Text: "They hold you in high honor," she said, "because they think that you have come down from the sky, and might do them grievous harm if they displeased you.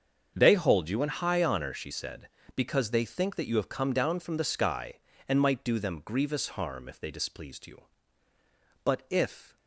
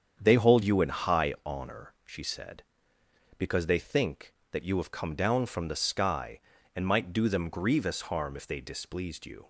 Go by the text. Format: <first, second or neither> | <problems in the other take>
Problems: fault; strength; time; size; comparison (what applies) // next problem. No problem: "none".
second | starts louder than the rest; until 1.3 s; 7 dB; strong in the second // goes on to say "But if"; noticeable; from 8.8 s on; 0.72 s long